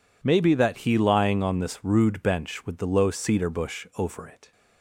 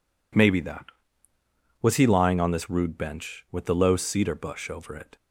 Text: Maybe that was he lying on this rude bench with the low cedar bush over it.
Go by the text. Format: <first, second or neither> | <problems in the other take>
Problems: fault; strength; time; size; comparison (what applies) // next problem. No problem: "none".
second | skips "was"; at 0.7 s